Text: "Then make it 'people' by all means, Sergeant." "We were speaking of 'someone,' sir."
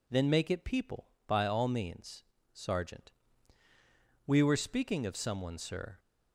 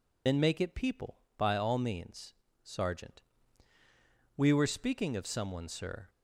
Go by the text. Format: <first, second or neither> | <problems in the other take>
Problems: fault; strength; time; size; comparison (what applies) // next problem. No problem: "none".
first | loses the start of "Then"; at 0.2 s; 65 ms